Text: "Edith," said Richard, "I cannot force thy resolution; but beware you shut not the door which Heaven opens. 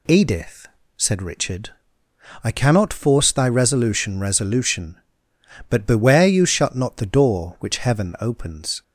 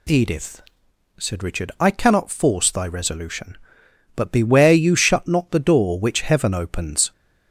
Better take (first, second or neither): second